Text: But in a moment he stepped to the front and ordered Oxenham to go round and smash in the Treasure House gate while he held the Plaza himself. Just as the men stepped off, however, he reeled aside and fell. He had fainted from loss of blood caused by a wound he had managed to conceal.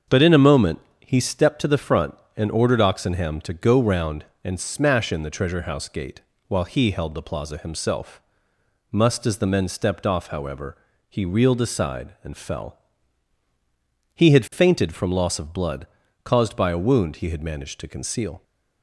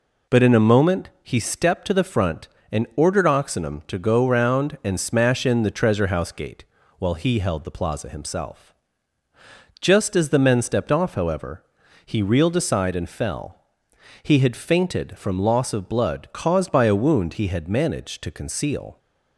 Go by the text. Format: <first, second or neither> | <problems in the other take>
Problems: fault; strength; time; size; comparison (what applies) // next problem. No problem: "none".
second | starts louder than the rest; until 1.3 s; 7 dB // pauses between "moment" and "he"; slight; at 0.7 s; 0.22 s long // pauses between "gate" and "while"; slight; at 6.2 s; 0.26 s long; slight in the second // says "Must" for "Just"; at 8.9 s // pauses between "blood" and "caused"; slight; at 15.8 s; 0.36 s long